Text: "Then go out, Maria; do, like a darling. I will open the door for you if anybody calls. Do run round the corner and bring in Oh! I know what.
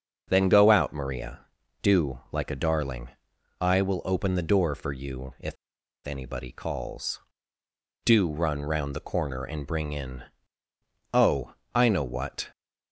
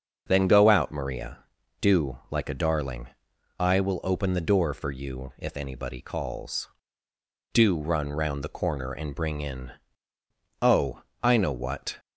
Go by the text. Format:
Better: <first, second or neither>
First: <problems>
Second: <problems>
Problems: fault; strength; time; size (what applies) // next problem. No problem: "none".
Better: second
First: starts louder than the rest; until 1.2 s; 7 dB // pauses between "if" and "anybody"; noticeable; at 5.5 s; 0.51 s long // pauses between "in" and "Oh"; noticeable; at 10.2 s; 0.90 s long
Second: starts louder than the rest; until 1.2 s; 6.5 dB // pauses between "in" and "Oh"; noticeable; at 9.7 s; 0.90 s long